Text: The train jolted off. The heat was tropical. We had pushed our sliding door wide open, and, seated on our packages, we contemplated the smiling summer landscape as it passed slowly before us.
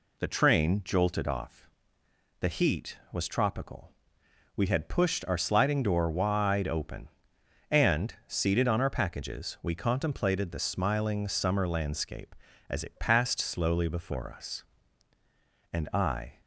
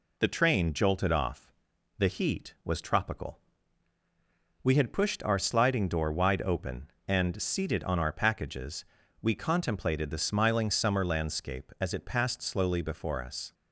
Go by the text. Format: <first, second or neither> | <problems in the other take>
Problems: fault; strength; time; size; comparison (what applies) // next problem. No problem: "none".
second | goes on to say "And I"; noticeable; from 15.7 s on; 0.70 s long